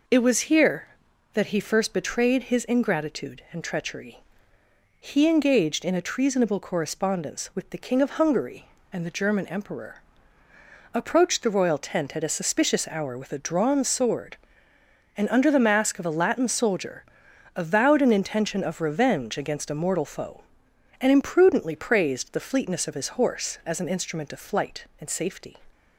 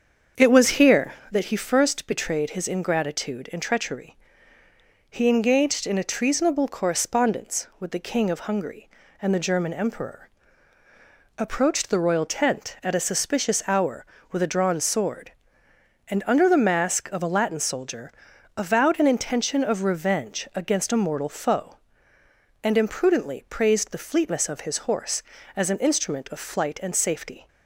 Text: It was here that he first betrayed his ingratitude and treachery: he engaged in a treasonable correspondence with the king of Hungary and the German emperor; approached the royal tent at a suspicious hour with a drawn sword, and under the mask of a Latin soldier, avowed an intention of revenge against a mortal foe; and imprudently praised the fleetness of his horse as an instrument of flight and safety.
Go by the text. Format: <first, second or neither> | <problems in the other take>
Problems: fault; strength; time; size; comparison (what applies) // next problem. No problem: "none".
first | starts louder than the rest; until 1.5 s; 7 dB